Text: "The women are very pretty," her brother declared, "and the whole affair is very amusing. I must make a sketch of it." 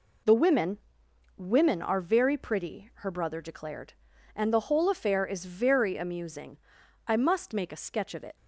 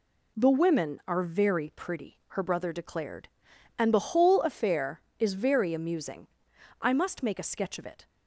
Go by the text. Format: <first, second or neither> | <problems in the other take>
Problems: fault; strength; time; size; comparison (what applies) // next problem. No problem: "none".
second | says "women" twice; at 1.3 s